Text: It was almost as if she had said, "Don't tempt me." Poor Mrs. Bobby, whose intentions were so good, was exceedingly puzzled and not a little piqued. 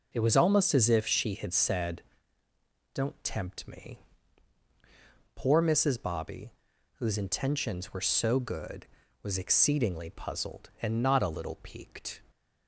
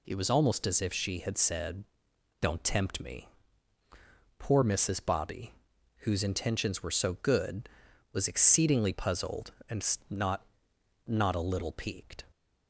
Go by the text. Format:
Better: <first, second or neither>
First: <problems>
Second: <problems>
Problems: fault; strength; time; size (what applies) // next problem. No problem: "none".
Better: first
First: none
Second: says "not" twice; at 11.0 s